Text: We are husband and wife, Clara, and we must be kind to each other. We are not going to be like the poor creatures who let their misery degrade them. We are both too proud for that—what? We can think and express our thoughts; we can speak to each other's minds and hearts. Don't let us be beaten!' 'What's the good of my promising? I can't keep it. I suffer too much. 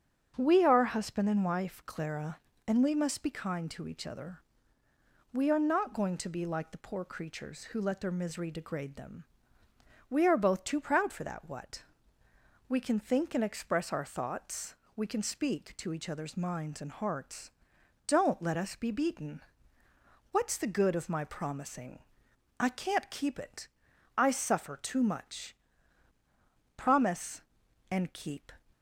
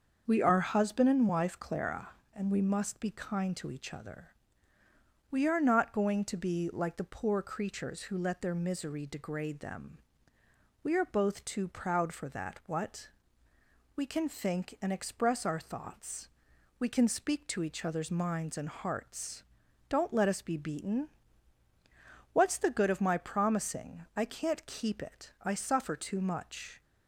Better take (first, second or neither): second